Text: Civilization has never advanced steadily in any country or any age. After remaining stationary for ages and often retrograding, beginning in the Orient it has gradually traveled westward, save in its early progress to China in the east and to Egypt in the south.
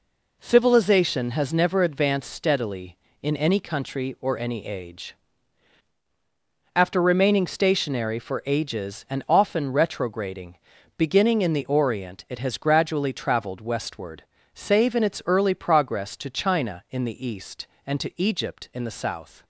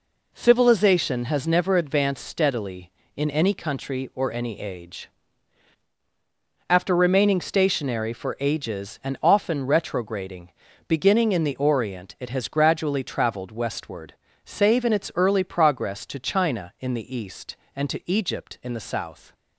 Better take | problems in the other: neither | none

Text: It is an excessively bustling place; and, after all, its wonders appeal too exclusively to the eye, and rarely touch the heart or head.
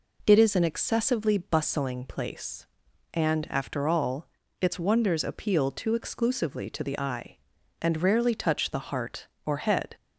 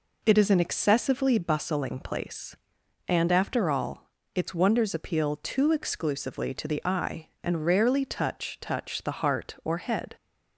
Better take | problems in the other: first | says "touch" twice; at 8.6 s

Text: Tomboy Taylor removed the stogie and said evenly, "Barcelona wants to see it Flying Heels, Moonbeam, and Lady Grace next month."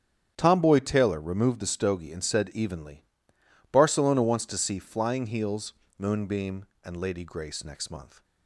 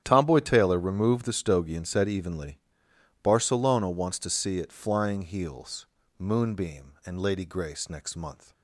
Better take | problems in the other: second | starts louder than the rest; strong; until 1.3 s; 9 dB; strong in the second // skips "it"; at 4.7 s

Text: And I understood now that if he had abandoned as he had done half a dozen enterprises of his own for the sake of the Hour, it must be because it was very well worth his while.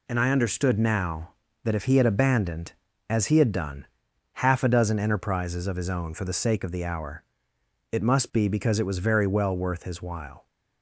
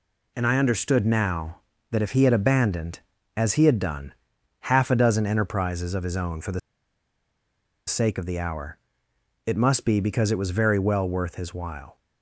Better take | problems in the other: first | pauses between "done" and "half"; noticeable; at 4.1 s; 0.52 s long; noticeable in the first // pauses between "the" and "sake"; strong; at 6.5 s; 1.2 s long

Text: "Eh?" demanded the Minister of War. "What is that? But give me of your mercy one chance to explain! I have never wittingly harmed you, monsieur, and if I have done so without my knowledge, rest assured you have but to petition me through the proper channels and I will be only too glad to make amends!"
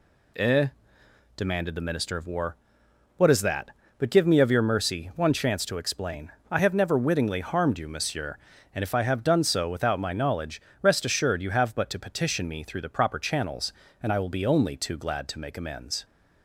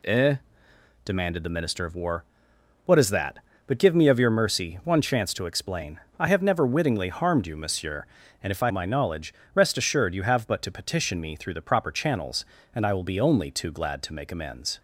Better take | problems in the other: first | skips "have done so without"; at 8.7 s

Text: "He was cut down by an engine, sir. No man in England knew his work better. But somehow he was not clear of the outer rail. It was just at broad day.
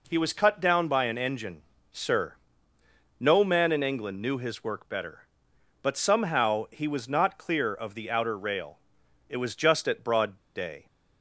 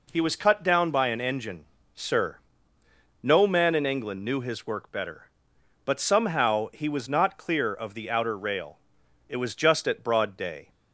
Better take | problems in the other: second | pauses between "broad" and "day"; slight; at 10.3 s; 0.17 s long

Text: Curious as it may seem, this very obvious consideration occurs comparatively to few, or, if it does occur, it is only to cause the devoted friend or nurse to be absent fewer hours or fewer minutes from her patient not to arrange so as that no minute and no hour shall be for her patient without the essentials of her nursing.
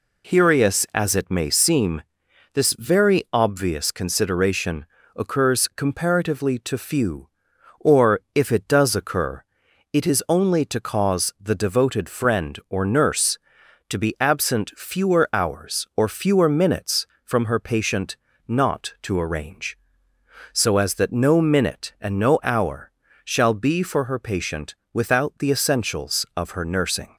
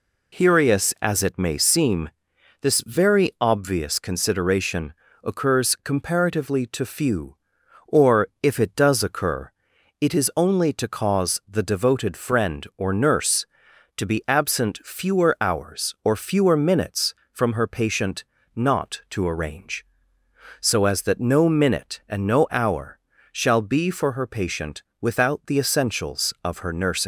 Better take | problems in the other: first | pauses between "consideration" and "occurs"; slight; at 4.9 s; 0.30 s long; slight in the first // pauses between "patient" and "not"; slight; at 18.2 s; 0.32 s long; slight in the first // pauses between "hour" and "shall"; slight; at 22.9 s; 0.34 s long; slight in the first // pauses between "patient" and "without"; slight; at 24.8 s; 0.18 s long; slight in the first // leaves "nursing" unfinished; at 27.0 s; 155 ms

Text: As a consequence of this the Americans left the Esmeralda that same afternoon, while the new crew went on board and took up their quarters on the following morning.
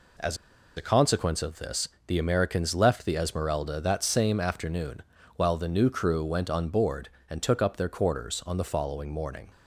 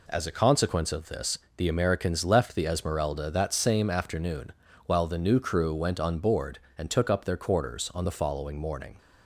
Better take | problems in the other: second | pauses between "As" and "a"; at 0.3 s; 0.41 s long // pauses between "this" and "the"; slight; at 1.8 s; 0.20 s long; slight in the second

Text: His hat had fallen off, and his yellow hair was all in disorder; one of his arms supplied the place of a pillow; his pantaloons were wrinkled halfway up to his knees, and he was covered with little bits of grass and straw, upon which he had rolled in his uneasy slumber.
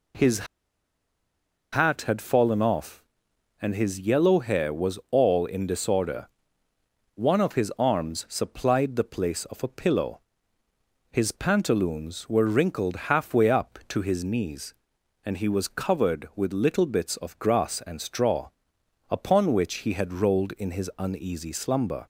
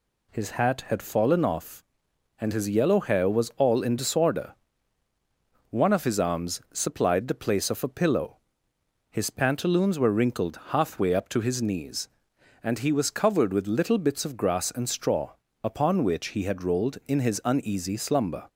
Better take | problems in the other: second | pauses between "His" and "hat"; strong; at 0.4 s; 1.2 s long

